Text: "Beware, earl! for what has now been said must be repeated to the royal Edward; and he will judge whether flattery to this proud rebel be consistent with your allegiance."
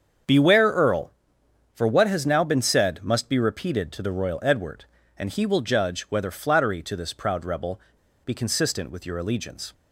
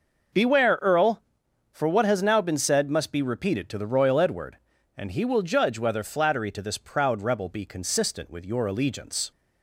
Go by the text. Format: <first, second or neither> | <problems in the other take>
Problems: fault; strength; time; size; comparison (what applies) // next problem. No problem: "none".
second | starts louder than the rest; strong; until 1.9 s; 7 dB // pauses between "rebel" and "be"; noticeable; at 7.7 s; 0.46 s long